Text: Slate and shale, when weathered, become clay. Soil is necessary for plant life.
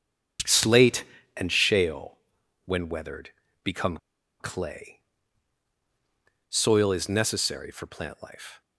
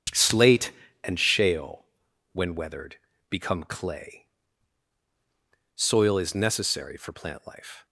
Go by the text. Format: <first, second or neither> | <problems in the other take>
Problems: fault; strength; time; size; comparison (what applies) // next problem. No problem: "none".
second | starts louder than the rest; strong; until 1.7 s; 7.5 dB; strong in the second // pauses between "become" and "clay"; at 3.9 s; 0.43 s long